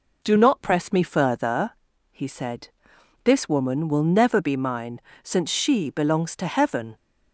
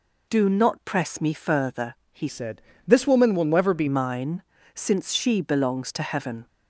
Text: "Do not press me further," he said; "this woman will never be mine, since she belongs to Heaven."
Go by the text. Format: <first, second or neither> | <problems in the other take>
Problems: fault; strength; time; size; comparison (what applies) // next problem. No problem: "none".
first | changes voice from "said" to "be"; from 2.2 to 3.8 s; 1.6 s long